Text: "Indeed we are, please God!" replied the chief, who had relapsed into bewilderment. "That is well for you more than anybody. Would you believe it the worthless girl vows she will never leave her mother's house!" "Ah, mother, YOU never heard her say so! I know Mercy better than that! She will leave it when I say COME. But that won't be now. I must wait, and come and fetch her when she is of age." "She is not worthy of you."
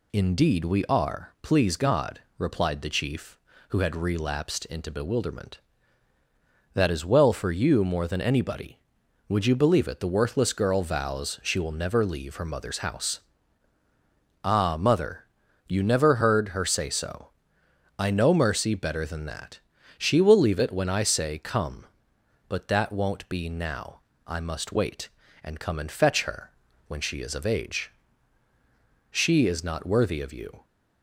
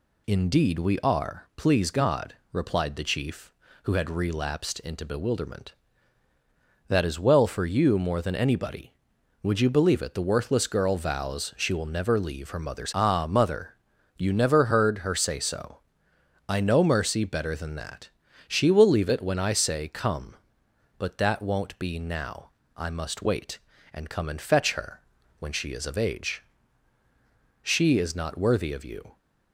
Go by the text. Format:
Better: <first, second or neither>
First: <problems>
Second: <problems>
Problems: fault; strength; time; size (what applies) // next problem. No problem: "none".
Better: first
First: pauses between "her" and "when"; slight; at 26.5 s; 0.34 s long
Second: skips "house"; at 12.9 s // pauses between "her" and "when"; slight; at 25.0 s; 0.36 s long